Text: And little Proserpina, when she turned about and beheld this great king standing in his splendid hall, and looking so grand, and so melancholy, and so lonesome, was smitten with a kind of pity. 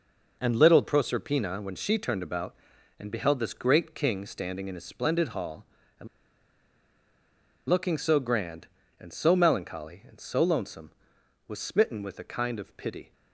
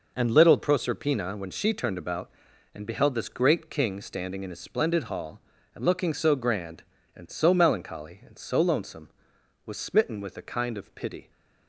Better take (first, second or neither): second